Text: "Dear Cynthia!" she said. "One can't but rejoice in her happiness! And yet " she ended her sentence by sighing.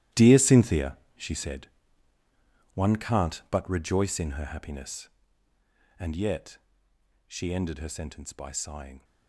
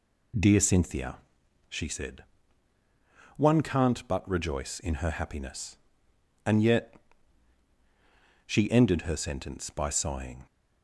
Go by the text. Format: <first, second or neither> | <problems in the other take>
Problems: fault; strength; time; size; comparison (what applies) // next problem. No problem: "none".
second | gets quieter; strong; throughout; 18 dB